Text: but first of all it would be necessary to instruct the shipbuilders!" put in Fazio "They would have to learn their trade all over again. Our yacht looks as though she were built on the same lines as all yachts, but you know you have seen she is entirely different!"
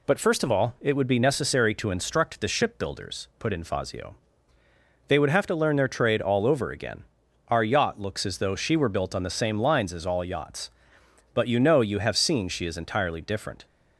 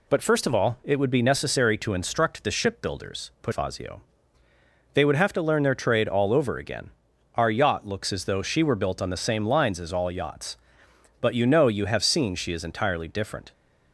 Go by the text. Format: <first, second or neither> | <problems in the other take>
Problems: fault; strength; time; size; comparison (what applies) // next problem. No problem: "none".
first | skips "in"; at 3.5 s // pauses between "Fazio" and "They"; noticeable; at 4.0 s; 0.90 s long; noticeable in the first